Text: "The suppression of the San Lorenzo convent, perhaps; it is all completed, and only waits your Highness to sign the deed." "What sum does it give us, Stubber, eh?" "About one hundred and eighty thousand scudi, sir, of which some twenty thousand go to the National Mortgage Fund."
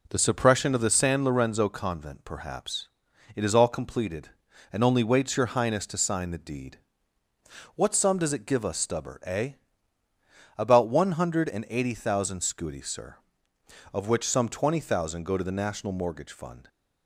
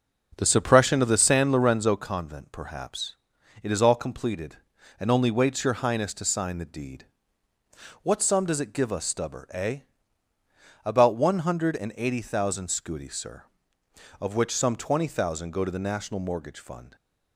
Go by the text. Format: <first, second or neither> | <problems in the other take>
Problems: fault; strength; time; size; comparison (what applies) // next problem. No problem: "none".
first | starts louder than the rest; noticeable; until 2.1 s; 6 dB